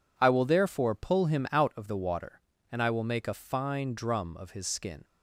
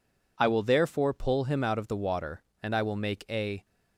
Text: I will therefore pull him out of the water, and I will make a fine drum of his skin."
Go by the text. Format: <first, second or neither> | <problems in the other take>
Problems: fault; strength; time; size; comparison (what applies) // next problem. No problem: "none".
first | stops before "fine drum of his skin"; at 3.6 s